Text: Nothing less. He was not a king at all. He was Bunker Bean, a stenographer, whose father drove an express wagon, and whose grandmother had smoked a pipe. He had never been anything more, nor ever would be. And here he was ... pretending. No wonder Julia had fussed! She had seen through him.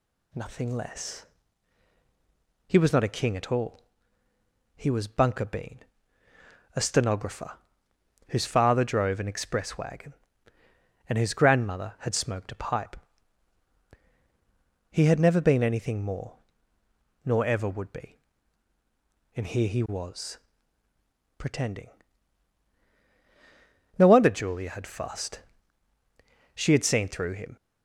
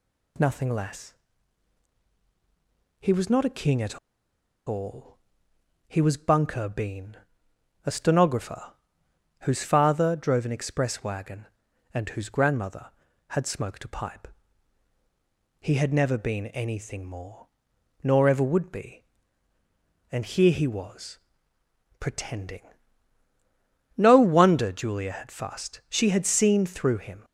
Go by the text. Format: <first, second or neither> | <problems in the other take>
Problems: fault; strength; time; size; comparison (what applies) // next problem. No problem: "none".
first | pauses between "at" and "all"; noticeable; at 3.9 s; 0.67 s long